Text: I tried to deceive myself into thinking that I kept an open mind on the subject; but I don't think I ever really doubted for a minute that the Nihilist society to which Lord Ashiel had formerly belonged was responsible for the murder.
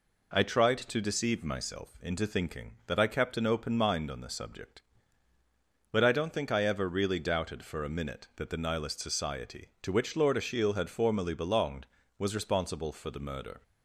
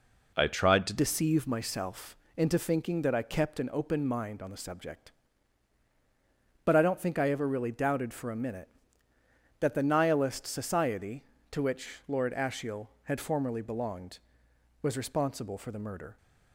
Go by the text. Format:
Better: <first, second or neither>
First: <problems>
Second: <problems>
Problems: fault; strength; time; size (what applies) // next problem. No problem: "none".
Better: first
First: none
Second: changes voice at "deceive"; from 0.9 s on; 15.2 s long // pauses between "myself" and "into"; slight; at 2.1 s; 0.18 s long